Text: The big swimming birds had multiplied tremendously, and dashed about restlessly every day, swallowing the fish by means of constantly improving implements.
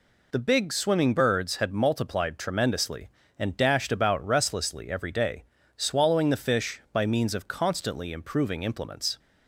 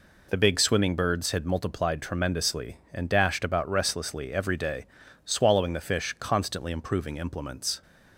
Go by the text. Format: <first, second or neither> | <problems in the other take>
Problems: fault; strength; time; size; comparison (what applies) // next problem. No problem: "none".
first | skips "by means of"; at 6.1 s